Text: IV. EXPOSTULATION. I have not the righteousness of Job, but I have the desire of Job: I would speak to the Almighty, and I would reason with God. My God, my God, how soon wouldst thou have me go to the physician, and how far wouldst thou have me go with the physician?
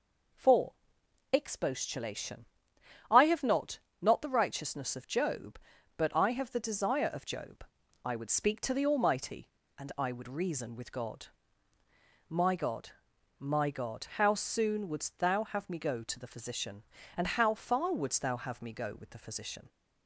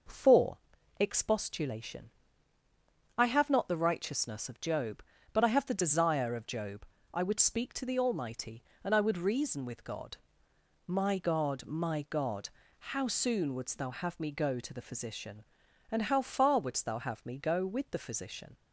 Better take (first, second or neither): second